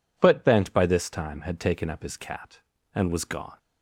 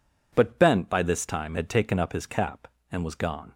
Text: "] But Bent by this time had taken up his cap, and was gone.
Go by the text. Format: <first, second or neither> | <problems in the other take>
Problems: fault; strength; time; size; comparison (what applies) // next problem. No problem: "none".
second | says "cat" for "cap"; at 2.1 s